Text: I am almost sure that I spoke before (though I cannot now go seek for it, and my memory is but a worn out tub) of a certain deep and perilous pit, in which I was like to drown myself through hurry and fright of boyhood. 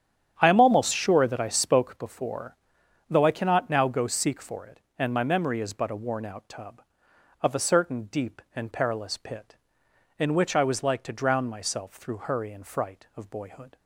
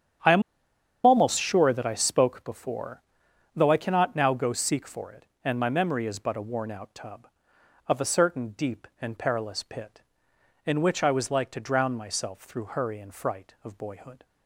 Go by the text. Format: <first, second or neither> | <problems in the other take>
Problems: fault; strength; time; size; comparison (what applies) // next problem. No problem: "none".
first | starts louder than the rest; strong; until 1.8 s; 8.5 dB; strong in the first // pauses between "am" and "almost"; noticeable; at 0.4 s; 0.64 s long